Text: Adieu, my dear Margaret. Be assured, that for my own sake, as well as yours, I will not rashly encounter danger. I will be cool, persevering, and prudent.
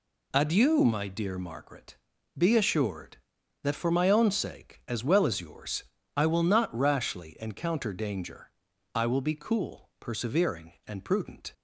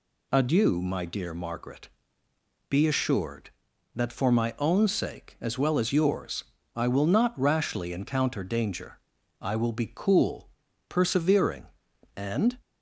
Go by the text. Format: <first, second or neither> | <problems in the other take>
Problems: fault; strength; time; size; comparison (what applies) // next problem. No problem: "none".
first | stops before "prudent"; at 12.6 s